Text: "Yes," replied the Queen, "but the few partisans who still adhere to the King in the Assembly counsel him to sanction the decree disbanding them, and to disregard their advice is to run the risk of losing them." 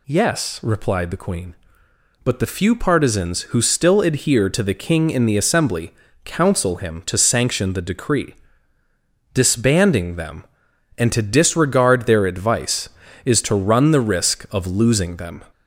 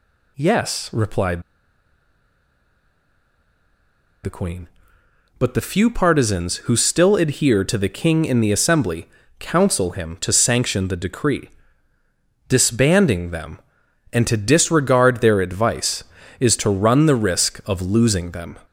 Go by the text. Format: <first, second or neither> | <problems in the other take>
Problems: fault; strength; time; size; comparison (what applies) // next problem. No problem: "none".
first | pauses between "replied" and "the"; strong; at 1.4 s; 2.8 s long // pauses between "Assembly" and "counsel"; slight; at 9.0 s; 0.28 s long; slight in the first // pauses between "decree" and "disbanding"; noticeable; at 11.4 s; 0.98 s long; noticeable in the first